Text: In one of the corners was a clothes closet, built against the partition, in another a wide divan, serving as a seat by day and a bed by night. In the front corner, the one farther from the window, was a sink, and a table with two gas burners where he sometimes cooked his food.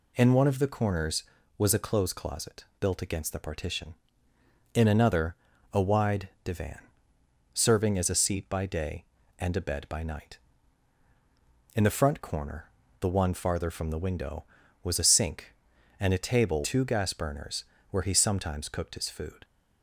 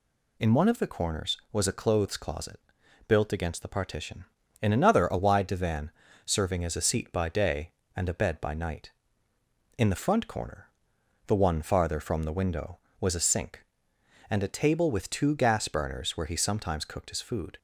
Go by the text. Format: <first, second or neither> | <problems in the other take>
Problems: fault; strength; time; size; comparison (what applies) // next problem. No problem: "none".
second | pauses between "another" and "a"; slight; at 5.3 s; 0.36 s long // pauses between "wide" and "divan"; slight; at 6.2 s; 0.16 s long // skips "with"; at 16.6 s // pauses between "burners" and "where"; slight; at 17.6 s; 0.26 s long